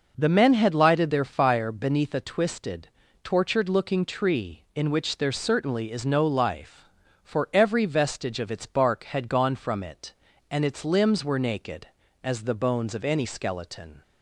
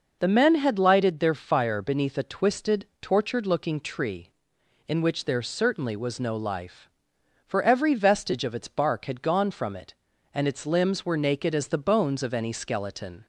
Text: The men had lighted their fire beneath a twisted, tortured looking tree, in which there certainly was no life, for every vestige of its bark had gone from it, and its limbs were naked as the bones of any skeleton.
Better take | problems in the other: second | says "is" for "was"; at 5.9 s

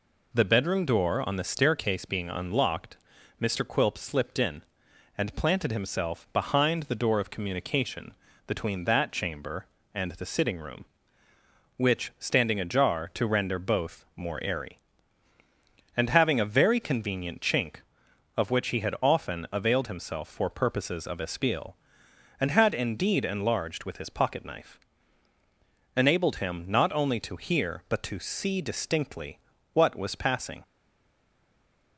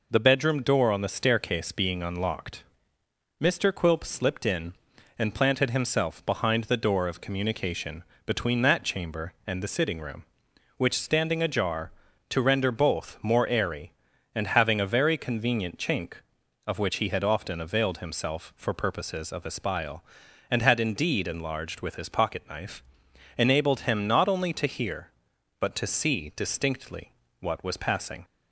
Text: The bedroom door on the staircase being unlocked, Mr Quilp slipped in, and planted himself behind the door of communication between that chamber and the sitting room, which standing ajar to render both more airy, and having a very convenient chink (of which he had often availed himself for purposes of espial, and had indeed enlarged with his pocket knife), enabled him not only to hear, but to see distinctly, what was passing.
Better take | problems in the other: second | pauses between "communication" and "between"; slight; at 8.1 s; 0.32 s long; slight in the second // stays silent after the last word; noticeable; from 30.6 s on; 1.3 s long

